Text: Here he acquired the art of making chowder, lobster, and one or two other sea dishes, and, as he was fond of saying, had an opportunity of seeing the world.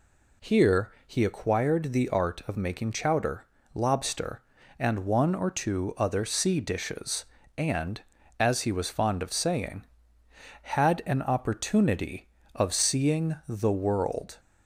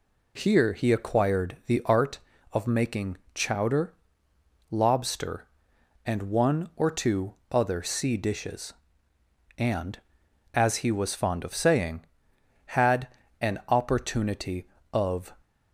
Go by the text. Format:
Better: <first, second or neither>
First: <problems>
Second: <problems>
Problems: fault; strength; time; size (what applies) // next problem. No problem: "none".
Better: first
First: none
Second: pauses between "making" and "chowder"; slight; at 3.1 s; 0.18 s long // pauses between "two" and "other"; slight; at 7.3 s; 0.16 s long // pauses between "had" and "an"; slight; at 13.0 s; 0.32 s long // stops before "seeing the world"; at 15.4 s